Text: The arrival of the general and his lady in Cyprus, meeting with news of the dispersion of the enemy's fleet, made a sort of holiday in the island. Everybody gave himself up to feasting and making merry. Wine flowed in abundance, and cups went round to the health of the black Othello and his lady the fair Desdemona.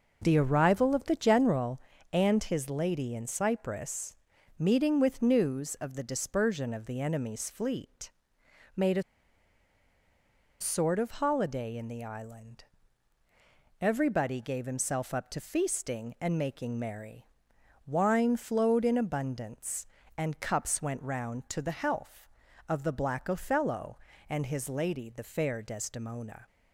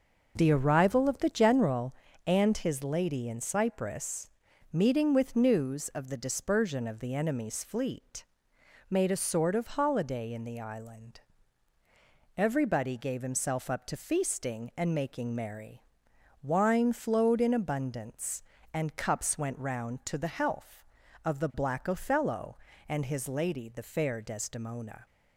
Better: second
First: pauses between "a" and "sort"; strong; at 9.0 s; 1.5 s long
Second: none

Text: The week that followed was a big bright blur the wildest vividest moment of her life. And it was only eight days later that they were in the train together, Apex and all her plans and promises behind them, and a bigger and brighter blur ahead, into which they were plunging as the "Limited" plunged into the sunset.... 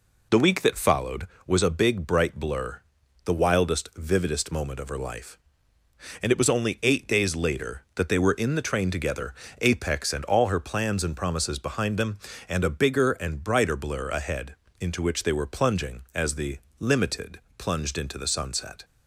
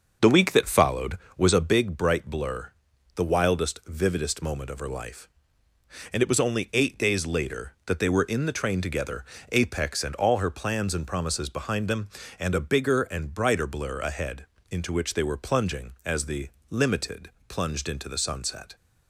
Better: first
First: pauses between "blur" and "the"; at 2.8 s; 0.44 s long // pauses between "the" and "Limited"; slight; at 16.5 s; 0.22 s long // pauses between "Limited" and "plunged"; slight; at 17.3 s; 0.20 s long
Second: starts louder than the rest; until 1.9 s; 6.5 dB // pauses between "blur" and "the"; at 2.7 s; 0.44 s long // pauses between "the" and "Limited"; slight; at 16.4 s; 0.22 s long // pauses between "Limited" and "plunged"; slight; at 17.2 s; 0.20 s long

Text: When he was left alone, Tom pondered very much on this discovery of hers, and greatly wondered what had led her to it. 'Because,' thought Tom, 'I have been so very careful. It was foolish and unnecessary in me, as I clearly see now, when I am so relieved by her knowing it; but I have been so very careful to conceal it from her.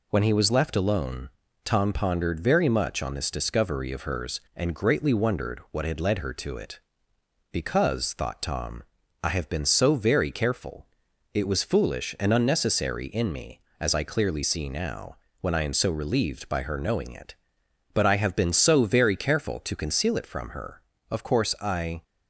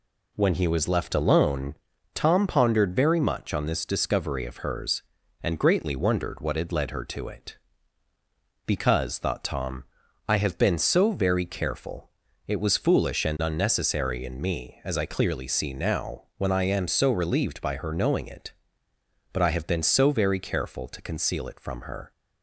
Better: second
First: goes on to say "Of course I"; noticeable; from 21.0 s on; 0.94 s long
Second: none

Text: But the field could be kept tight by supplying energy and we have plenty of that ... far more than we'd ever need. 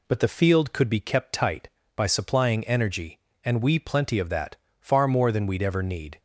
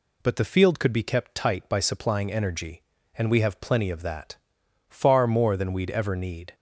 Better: second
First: skips "have"; at 3.7 s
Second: none

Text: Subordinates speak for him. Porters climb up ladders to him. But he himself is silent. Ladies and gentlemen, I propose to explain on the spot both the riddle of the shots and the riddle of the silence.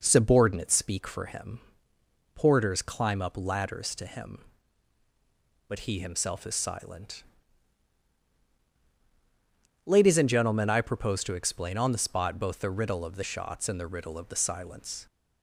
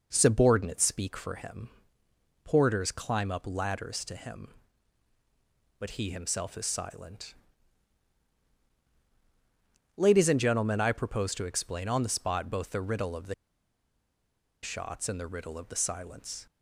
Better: first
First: none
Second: pauses between "the" and "shots"; strong; at 13.3 s; 1.2 s long

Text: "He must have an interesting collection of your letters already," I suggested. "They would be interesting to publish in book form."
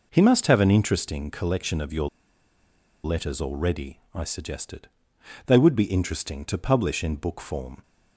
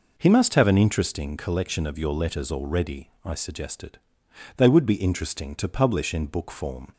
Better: second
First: pauses between "your" and "letters"; noticeable; at 2.0 s; 0.95 s long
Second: none

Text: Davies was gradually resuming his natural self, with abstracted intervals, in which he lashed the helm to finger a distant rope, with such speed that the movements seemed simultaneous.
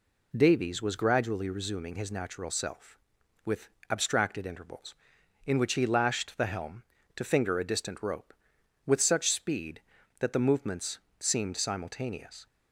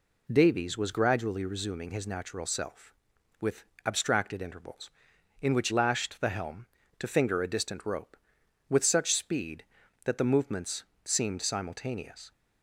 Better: first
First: pauses between "with" and "abstracted"; slight; at 3.6 s; 0.22 s long // pauses between "movements" and "seemed"; slight; at 10.9 s; 0.20 s long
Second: pauses between "with" and "abstracted"; slight; at 3.6 s; 0.22 s long // skips "he"; at 5.6 s // pauses between "movements" and "seemed"; slight; at 10.8 s; 0.20 s long

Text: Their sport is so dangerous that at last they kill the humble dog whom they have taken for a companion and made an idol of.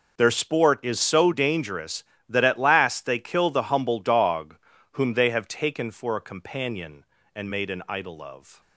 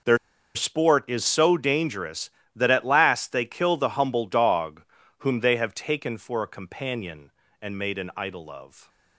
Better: first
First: pauses between "dog" and "whom"; slight; at 4.5 s; 0.36 s long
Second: pauses between "Their" and "sport"; at 0.1 s; 0.38 s long // pauses between "dog" and "whom"; slight; at 4.8 s; 0.36 s long

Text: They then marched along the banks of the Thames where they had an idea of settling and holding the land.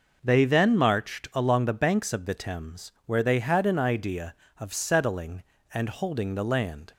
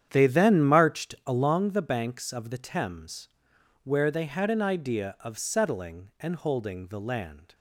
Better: first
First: none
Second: starts louder than the rest; strong; until 1.6 s; 9 dB // pauses between "Thames" and "where"; noticeable; at 3.2 s; 0.54 s long

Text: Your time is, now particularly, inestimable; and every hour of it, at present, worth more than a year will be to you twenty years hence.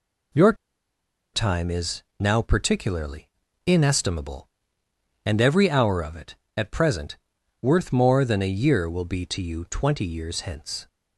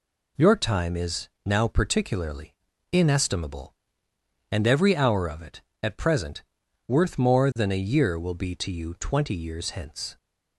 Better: second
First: pauses between "Your" and "time"; noticeable; at 0.5 s; 0.79 s long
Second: none

